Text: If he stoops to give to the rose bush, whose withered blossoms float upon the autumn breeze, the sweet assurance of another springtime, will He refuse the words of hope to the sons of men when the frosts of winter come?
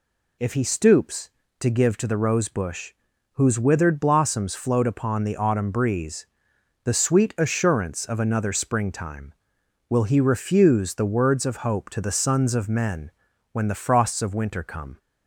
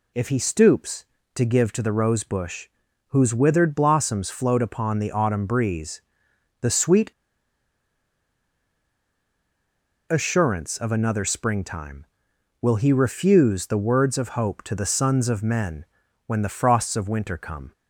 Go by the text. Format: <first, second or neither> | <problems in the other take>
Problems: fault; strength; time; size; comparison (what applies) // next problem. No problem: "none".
first | pauses between "sweet" and "assurance"; strong; at 7.1 s; 2.9 s long // pauses between "men" and "when"; at 15.8 s; 0.40 s long; also in the first